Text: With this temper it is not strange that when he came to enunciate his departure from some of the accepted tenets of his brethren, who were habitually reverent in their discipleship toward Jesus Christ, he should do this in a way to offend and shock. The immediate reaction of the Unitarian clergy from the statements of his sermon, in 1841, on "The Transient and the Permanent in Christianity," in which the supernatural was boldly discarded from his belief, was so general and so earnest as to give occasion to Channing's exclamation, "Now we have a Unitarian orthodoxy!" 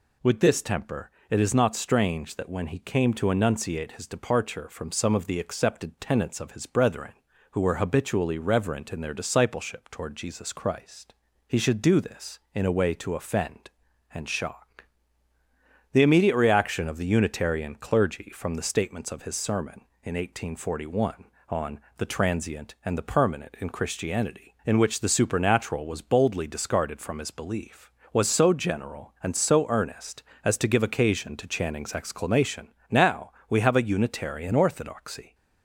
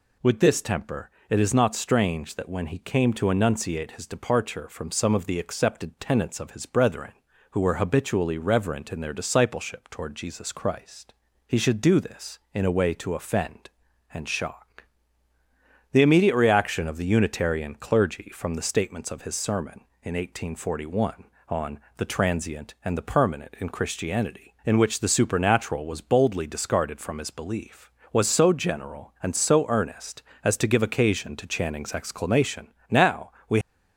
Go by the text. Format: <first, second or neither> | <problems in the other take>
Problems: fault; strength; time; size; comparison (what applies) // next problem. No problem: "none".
first | pauses between "temper" and "it"; slight; at 1.1 s; 0.20 s long; slight in the first // pauses between "on" and "The"; slight; at 21.7 s; 0.20 s long; slight in the first // pauses between "Now" and "we"; slight; at 33.3 s; 0.18 s long; slight in the first // stops before "have a Unitarian orthodoxy"; at 33.6 s